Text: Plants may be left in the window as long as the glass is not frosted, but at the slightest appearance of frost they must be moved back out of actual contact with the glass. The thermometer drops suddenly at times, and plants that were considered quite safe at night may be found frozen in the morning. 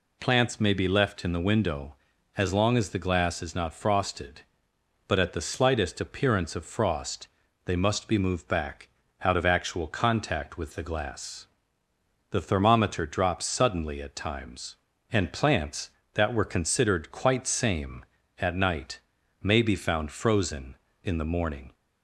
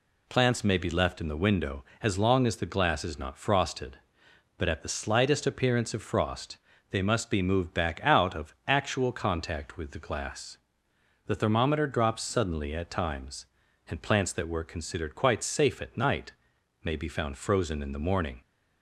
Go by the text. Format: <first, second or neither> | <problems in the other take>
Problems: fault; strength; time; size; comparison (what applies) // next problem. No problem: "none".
second | pauses between "frost" and "they"; at 7.2 s; 0.38 s long; slight in the second // pauses between "back" and "out"; slight; at 8.8 s; 0.34 s long // says "same" for "safe"; at 17.4 s // pauses between "night" and "may"; at 18.9 s; 0.42 s long; noticeable in the second